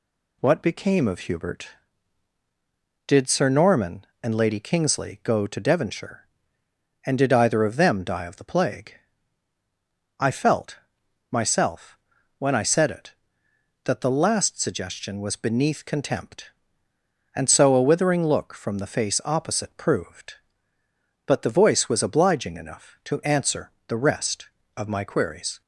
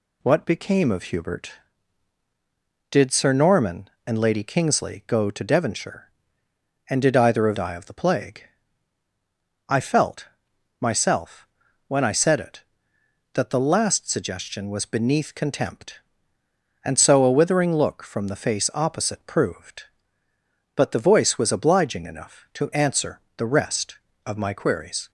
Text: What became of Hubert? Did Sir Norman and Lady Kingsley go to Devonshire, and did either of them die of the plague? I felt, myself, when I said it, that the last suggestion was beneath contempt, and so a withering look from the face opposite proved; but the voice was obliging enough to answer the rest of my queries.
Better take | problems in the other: first | skips "them"; at 7.5 s // pauses between "answer" and "the"; slight; at 23.2 s; 0.16 s long; slight in the first

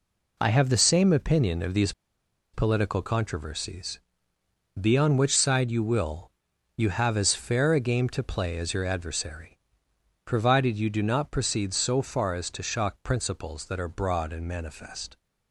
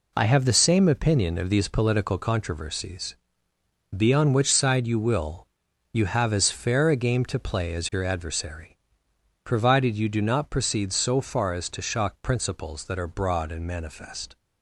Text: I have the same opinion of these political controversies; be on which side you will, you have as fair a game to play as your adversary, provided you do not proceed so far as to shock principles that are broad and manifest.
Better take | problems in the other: second | pauses between "these" and "political"; noticeable; at 1.9 s; 0.62 s long

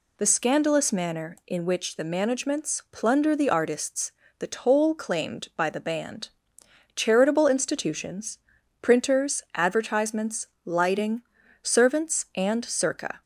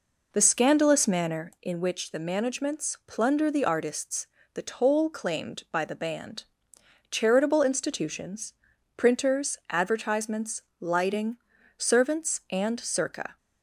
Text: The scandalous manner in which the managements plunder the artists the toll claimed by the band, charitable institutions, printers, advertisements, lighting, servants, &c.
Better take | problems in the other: first | starts louder than the rest; noticeable; until 1.5 s; 4 dB // pauses between "artists" and "the"; slight; at 4.2 s; 0.26 s long; slight in the first

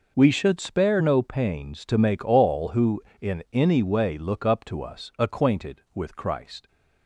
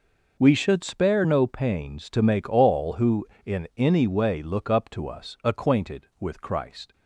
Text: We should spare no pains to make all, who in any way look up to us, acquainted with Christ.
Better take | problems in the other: neither | none

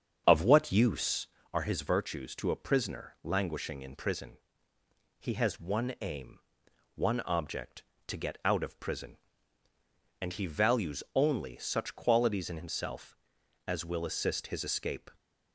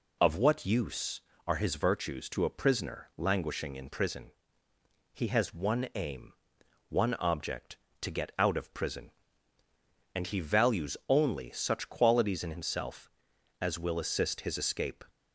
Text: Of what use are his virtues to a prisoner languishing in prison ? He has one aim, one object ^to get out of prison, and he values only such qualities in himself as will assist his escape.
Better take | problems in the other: second | starts louder than the rest; strong; until 1.5 s; 7.5 dB

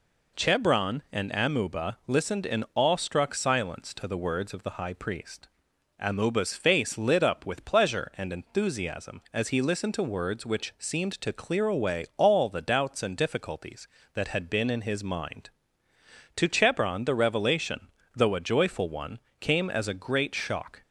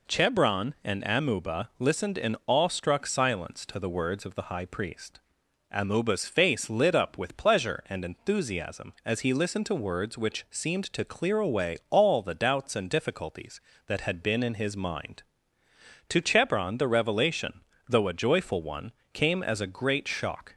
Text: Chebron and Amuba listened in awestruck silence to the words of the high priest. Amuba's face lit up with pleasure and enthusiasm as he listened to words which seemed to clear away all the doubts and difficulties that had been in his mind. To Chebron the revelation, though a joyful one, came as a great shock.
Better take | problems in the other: neither | none

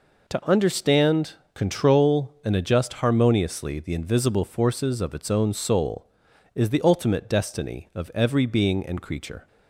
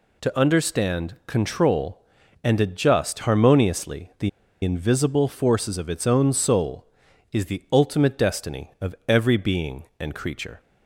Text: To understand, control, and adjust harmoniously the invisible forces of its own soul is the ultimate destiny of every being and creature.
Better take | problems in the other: first | pauses between "the" and "invisible"; slight; at 4.2 s; 0.34 s long

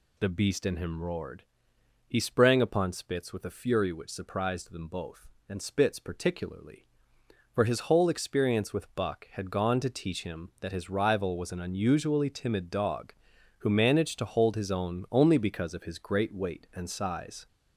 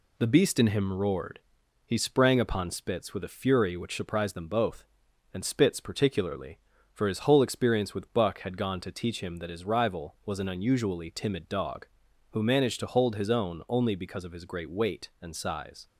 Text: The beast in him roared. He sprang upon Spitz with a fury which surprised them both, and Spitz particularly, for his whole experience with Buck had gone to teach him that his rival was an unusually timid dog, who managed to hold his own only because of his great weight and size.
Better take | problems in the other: second | gets louder; noticeable; throughout; 4 dB

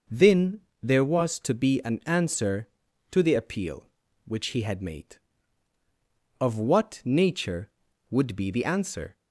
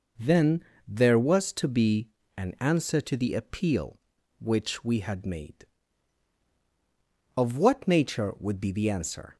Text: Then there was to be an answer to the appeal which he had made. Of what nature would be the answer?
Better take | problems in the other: first | pauses between "Then" and "there"; slight; at 0.6 s; 0.24 s long; slight in the first // pauses between "be" and "an"; slight; at 2.0 s; 0.28 s long // says "we" for "he"; at 4.8 s

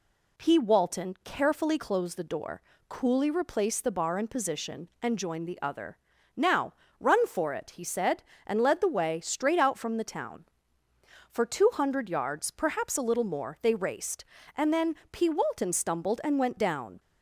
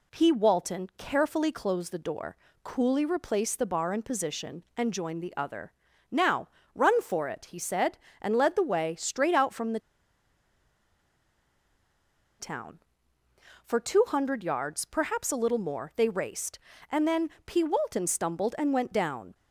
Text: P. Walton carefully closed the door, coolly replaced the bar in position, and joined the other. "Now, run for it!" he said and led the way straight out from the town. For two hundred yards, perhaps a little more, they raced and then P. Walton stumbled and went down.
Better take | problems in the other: first | pauses between "the" and "town"; strong; at 9.7 s; 2.6 s long // pauses between "then" and "P"; slight; at 17.2 s; 0.16 s long; slight in the first

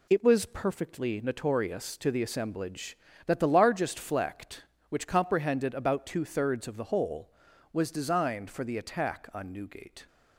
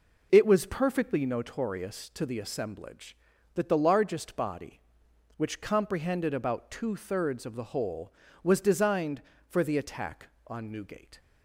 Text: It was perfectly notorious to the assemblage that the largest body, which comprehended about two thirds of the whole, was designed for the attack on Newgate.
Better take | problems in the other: second | says "flect" for "body"; at 3.9 s

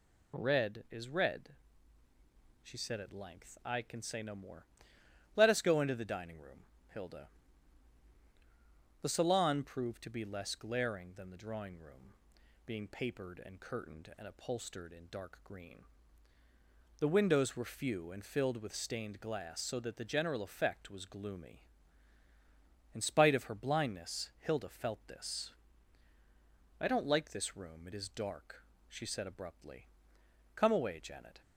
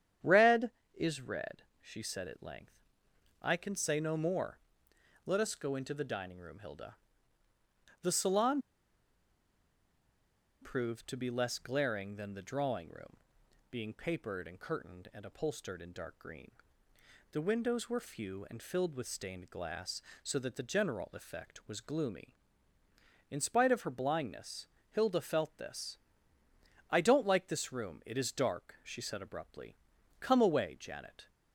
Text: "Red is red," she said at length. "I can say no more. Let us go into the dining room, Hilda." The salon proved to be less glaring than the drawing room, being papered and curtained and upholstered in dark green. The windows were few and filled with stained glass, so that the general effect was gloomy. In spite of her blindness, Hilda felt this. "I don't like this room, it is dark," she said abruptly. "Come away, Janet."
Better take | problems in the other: first | starts louder than the rest; strong; until 1.4 s; 9 dB // pauses between "salon" and "proved"; strong; at 8.6 s; 2.0 s long

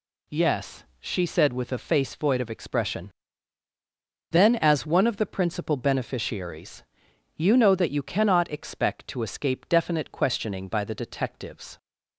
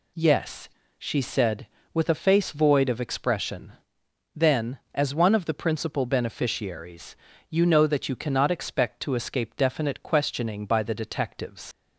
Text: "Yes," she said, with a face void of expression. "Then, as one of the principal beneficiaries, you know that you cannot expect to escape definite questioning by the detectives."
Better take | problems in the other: first | leaves "detectives" unfinished; at 11.7 s; 85 ms

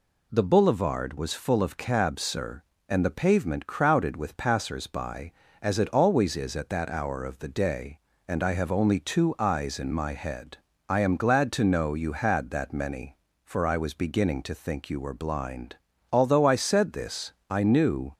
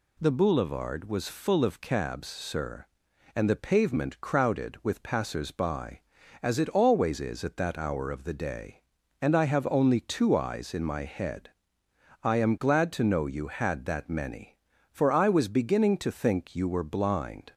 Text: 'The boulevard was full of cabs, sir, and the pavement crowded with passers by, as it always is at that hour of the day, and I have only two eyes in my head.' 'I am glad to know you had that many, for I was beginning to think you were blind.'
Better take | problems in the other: second | goes on to say "Although I said this I knew"; strong; from 16.1 s on; 2.0 s long

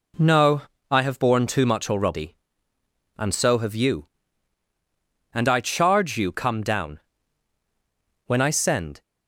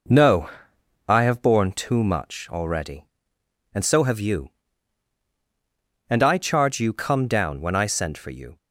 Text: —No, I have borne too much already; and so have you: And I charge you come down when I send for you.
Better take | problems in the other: second | pauses between "down" and "when"; at 7.0 s; 1.2 s long // stops before "for you"; at 9.0 s

